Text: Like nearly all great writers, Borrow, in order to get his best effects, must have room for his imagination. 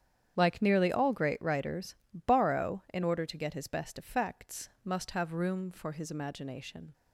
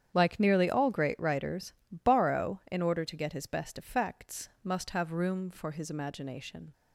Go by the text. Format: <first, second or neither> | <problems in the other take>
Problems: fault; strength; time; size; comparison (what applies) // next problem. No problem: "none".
neither | starts louder than the rest; strong; the same in both